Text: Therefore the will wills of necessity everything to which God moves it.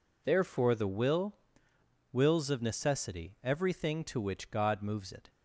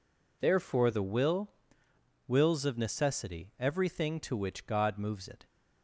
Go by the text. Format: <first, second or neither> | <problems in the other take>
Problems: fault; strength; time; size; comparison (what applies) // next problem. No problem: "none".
neither | pauses between "will" and "wills"; noticeable; the same in both